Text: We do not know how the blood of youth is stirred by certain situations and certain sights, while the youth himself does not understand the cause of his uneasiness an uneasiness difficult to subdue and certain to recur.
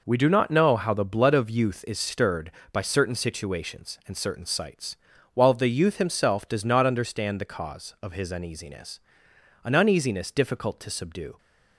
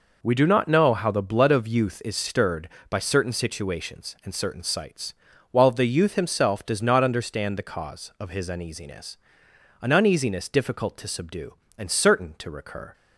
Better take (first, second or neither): second